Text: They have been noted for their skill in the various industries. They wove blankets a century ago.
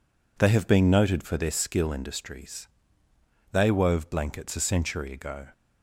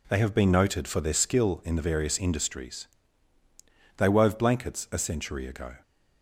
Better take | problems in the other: second | skips "in the various"; at 1.9 s

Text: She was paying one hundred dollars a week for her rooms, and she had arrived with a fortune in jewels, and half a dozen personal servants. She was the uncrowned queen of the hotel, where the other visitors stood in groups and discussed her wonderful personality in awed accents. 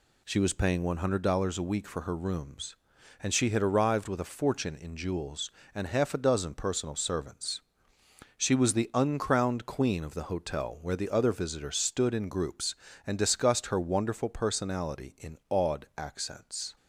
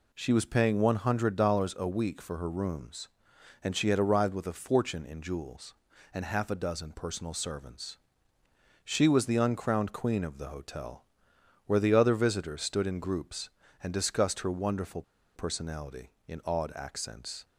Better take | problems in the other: first | pauses between "wonderful" and "personality"; slight; at 15.0 s; 0.34 s long

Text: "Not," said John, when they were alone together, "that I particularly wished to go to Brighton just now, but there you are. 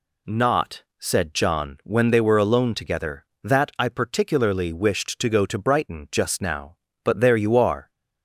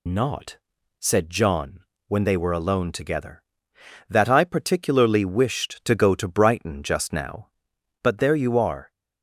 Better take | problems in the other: first | loses the start of "Not"; at 0.0 s; 75 ms

